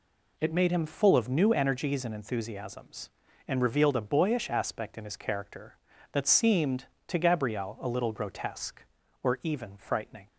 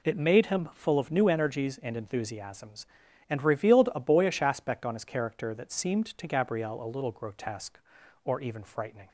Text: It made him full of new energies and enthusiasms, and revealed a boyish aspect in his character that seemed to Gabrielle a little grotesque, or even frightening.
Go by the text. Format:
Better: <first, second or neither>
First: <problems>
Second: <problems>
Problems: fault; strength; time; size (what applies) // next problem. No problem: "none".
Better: first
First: none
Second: says "on" for "in"; at 4.8 s